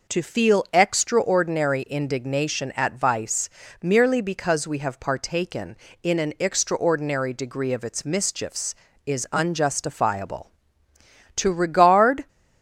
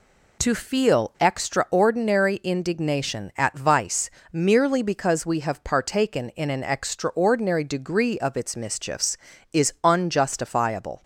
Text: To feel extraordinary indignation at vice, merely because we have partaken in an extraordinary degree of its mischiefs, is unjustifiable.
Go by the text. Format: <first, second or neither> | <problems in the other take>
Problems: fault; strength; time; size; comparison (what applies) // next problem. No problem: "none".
second | goes on to say "To regard"; noticeable; from 11.3 s on; 0.90 s long